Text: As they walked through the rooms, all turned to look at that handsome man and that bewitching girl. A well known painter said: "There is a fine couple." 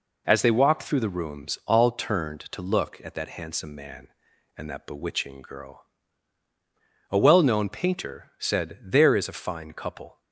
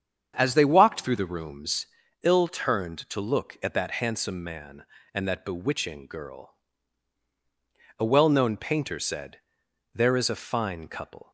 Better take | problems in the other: first | starts louder than the rest; strong; until 1.3 s; 8 dB // says "ill" for "all"; at 2.2 s

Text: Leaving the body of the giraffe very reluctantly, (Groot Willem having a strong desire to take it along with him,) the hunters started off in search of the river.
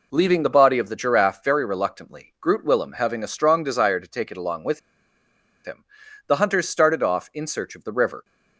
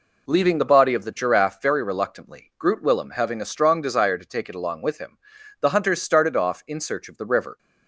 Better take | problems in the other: second | pauses between "with" and "him"; noticeable; at 4.7 s; 0.84 s long

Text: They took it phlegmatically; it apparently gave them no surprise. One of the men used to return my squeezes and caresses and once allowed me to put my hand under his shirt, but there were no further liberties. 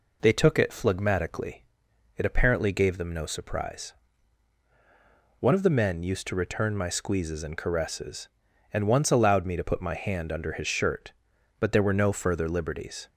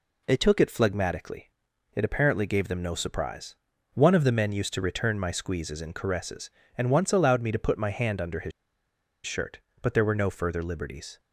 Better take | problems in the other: first | pauses between "his" and "shirt"; noticeable; at 8.5 s; 0.74 s long

